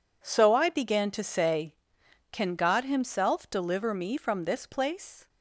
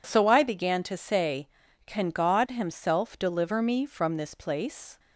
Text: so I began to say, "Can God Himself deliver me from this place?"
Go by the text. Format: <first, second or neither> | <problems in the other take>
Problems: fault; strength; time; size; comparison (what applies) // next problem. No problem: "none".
neither | none